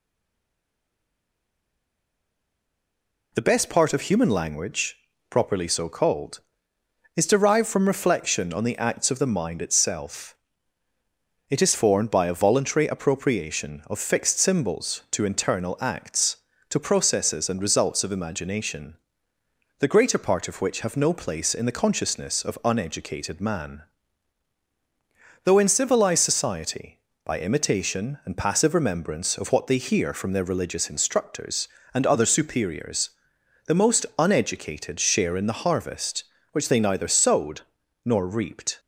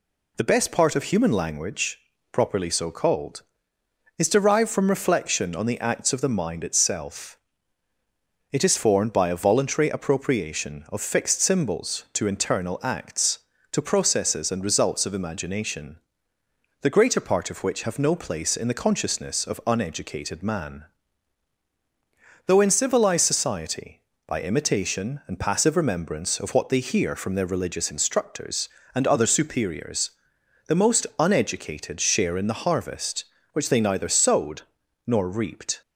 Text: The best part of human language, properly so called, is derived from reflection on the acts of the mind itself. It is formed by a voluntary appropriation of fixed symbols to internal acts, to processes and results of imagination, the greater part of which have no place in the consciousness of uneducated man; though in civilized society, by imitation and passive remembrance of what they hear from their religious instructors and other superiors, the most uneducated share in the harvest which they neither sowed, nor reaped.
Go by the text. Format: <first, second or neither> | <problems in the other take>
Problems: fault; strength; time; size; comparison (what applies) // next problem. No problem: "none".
second | stays silent before the first word; strong; until 3.3 s; 3.3 s long